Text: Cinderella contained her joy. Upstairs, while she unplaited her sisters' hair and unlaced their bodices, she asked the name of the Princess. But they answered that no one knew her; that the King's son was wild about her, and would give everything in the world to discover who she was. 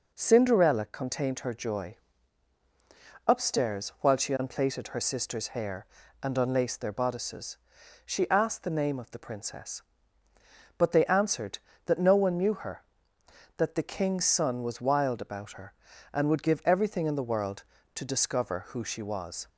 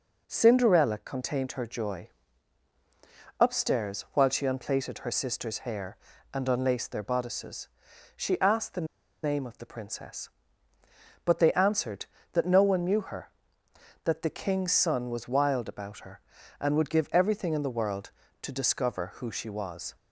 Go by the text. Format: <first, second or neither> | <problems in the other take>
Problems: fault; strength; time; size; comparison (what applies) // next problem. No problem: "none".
first | pauses between "the" and "name"; at 8.8 s; 0.38 s long